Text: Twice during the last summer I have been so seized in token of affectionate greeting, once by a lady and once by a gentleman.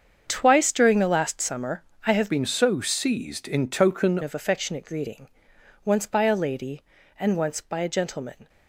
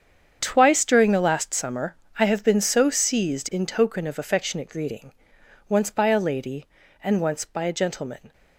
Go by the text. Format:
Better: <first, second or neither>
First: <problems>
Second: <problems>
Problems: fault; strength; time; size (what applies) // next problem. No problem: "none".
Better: second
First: starts louder than the rest; strong; until 1.2 s; 7 dB // pauses between "summer" and "I"; slight; at 1.8 s; 0.24 s long // changes voice from "been" to "token"; from 2.2 to 4.1 s; 1.9 s long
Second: starts louder than the rest; strong; until 1.4 s; 7.5 dB // pauses between "summer" and "I"; slight; at 1.9 s; 0.24 s long